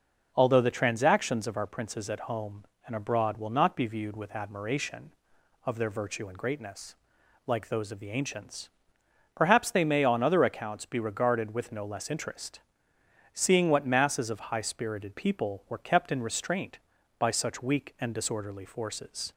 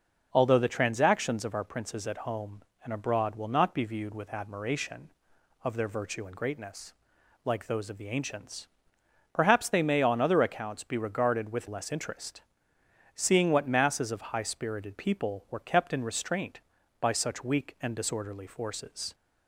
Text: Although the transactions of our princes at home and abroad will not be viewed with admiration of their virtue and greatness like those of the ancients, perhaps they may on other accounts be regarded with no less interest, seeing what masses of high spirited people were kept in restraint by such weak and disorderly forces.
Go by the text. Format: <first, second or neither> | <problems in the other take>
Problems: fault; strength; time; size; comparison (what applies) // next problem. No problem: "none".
first | pauses between "greatness" and "like"; noticeable; at 6.9 s; 0.52 s long; noticeable in the first // skips "no"; at 11.6 s